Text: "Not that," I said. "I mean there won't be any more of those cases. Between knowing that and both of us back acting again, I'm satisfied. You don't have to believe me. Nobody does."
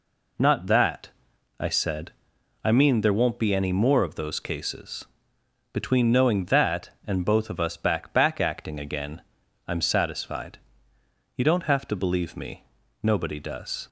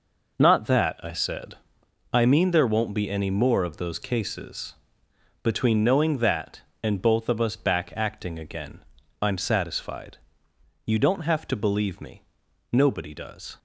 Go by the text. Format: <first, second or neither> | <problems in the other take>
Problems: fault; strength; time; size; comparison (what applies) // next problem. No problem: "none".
second | says "back" twice; at 8.1 s